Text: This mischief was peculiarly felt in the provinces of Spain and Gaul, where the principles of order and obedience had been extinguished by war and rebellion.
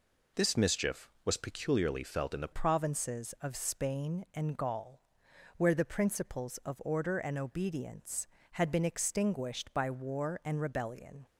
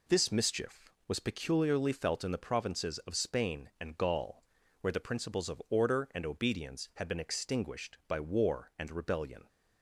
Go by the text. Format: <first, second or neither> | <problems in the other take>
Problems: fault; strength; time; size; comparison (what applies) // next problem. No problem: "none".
second | changes voice at "provinces"; from 2.5 s on; 8.7 s long